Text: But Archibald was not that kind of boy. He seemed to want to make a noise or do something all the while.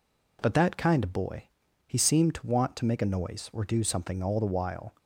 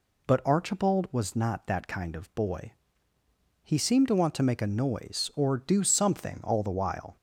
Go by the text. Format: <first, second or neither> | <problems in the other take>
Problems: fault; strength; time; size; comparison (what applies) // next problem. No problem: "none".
second | skips "Archibald was not"; at 0.5 s